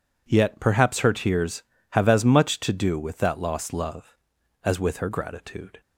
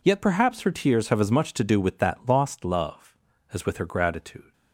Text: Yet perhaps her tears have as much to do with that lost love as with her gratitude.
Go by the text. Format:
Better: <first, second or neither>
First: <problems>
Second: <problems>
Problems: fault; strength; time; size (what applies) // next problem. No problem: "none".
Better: neither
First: none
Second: none